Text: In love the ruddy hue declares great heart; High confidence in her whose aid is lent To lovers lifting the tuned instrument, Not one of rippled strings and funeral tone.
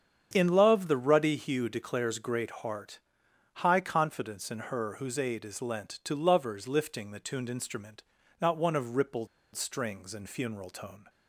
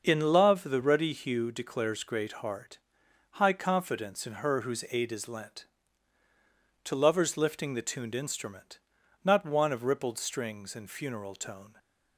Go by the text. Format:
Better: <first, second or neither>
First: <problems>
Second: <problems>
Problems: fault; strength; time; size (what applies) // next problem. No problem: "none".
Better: second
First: starts louder than the rest; strong; until 1.3 s; 8 dB // pauses between "rippled" and "strings"; slight; at 9.2 s; 0.27 s long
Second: starts louder than the rest; until 1.0 s; 6 dB